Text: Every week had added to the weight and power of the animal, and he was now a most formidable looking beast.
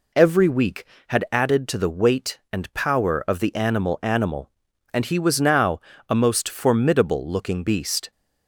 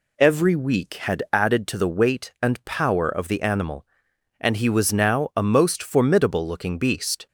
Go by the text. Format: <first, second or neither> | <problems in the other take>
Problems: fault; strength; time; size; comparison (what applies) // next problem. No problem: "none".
second | says "animal" twice; at 4.0 s // pauses between "now" and "a"; slight; at 5.7 s; 0.30 s long